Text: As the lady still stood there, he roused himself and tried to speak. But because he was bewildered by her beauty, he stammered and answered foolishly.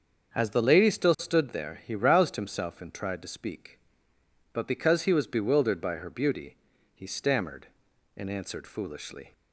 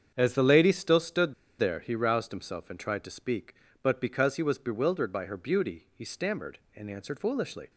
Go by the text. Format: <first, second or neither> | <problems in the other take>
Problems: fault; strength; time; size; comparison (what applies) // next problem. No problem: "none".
first | starts louder than the rest; strong; until 1.1 s; 7.5 dB; also in the first // pauses between "stood" and "there"; slight; at 1.3 s; 0.26 s long